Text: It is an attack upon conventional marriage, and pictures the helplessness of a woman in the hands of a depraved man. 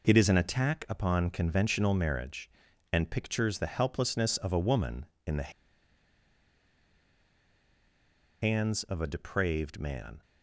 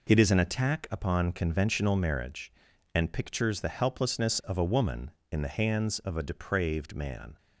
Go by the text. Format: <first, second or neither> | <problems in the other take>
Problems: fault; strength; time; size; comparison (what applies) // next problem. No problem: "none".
second | pauses between "the" and "hands"; strong; at 5.4 s; 2.9 s long